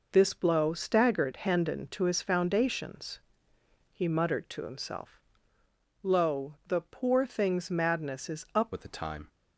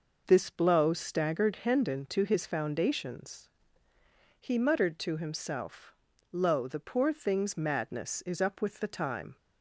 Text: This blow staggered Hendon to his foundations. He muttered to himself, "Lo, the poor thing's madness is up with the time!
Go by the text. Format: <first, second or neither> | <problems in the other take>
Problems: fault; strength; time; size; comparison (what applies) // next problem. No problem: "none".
second | changes voice at "with"; from 8.7 s on; 0.5 s long